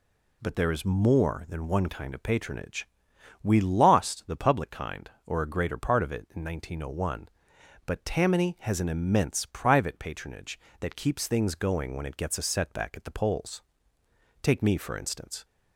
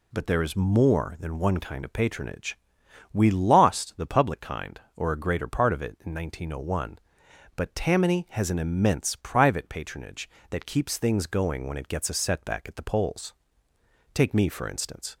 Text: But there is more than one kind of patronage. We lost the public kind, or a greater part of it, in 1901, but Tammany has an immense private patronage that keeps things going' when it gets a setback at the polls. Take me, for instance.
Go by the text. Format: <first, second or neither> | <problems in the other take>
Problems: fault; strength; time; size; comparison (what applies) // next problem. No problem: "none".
neither | none